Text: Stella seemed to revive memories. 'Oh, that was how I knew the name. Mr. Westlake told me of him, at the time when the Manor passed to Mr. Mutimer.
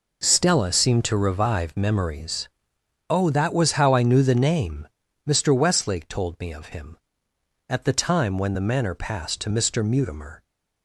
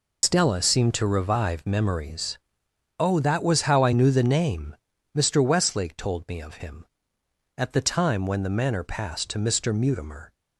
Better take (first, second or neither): first